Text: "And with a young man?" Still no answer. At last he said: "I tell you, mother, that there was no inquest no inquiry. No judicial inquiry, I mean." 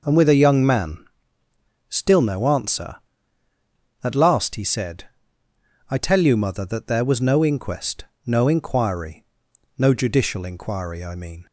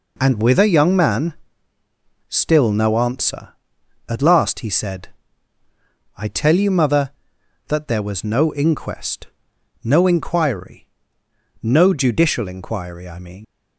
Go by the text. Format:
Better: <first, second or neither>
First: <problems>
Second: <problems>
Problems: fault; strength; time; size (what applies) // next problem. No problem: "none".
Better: first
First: pauses between "inquest" and "no"; slight; at 8.0 s; 0.18 s long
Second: pauses between "inquest" and "no"; noticeable; at 9.2 s; 0.56 s long // leaves "mean" unfinished; at 13.4 s; 85 ms